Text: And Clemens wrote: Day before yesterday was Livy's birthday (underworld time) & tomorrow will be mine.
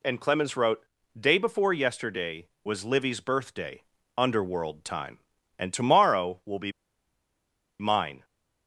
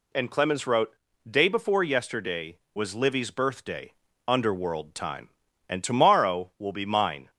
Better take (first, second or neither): second